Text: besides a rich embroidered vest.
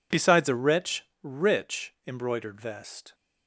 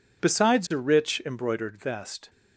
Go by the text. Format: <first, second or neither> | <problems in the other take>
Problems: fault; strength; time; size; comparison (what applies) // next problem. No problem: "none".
second | says "rich" twice; at 1.2 s